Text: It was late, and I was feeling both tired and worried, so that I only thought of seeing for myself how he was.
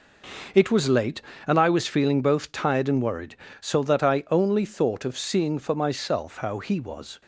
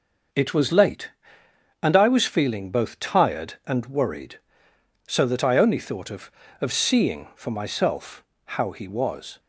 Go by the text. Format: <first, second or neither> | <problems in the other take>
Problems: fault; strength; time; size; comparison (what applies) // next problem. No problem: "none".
first | starts louder than the rest; until 2.0 s; 6.5 dB // says "of" twice; at 6.6 s // pauses between "myself" and "how"; slight; at 8.2 s; 0.22 s long